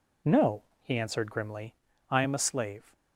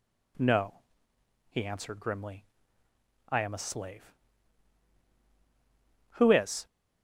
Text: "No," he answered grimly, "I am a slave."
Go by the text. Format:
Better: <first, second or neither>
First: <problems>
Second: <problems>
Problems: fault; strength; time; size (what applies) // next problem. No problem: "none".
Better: first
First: none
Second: goes on to say "Who is"; from 6.1 s on; 0.52 s long